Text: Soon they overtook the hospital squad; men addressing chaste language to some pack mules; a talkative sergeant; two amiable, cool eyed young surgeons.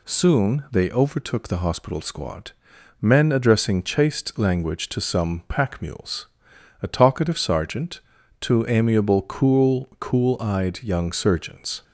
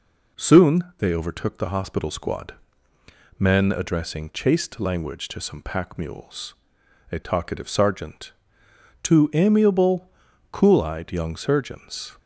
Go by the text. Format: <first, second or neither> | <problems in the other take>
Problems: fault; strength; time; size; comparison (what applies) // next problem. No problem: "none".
second | says "cool" twice; at 9.9 s